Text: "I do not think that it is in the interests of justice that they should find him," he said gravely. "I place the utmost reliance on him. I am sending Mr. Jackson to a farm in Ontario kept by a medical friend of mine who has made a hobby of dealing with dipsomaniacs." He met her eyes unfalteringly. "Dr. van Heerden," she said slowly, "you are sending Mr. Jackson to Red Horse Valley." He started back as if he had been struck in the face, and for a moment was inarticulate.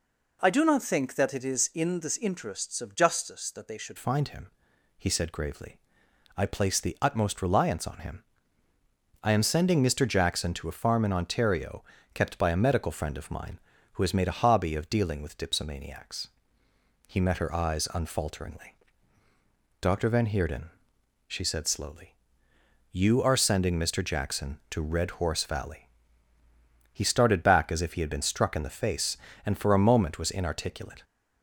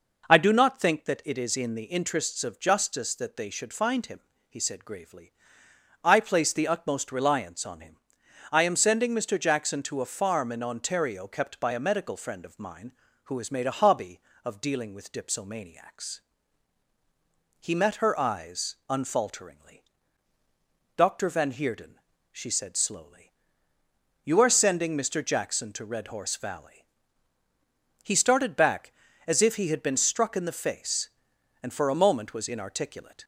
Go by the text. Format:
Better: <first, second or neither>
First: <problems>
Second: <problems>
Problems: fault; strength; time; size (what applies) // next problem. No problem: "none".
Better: second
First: changes voice at "find"; from 3.9 s on; 27.1 s long // pauses between "Ontario" and "kept"; slight; at 11.8 s; 0.30 s long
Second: none